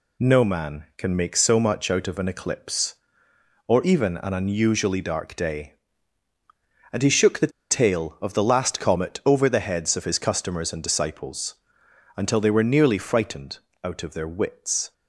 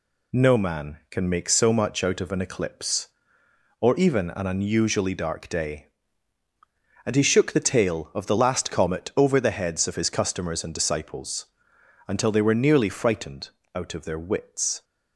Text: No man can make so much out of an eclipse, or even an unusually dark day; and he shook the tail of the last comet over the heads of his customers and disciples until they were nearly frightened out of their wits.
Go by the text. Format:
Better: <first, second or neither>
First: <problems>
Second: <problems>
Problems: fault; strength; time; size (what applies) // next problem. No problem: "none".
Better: second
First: pauses between "the" and "tail"; slight; at 7.4 s; 0.20 s long // pauses between "disciples" and "until"; noticeable; at 11.5 s; 0.60 s long // pauses between "frightened" and "out"; slight; at 13.5 s; 0.26 s long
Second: pauses between "disciples" and "until"; noticeable; at 11.4 s; 0.60 s long // pauses between "frightened" and "out"; slight; at 13.4 s; 0.26 s long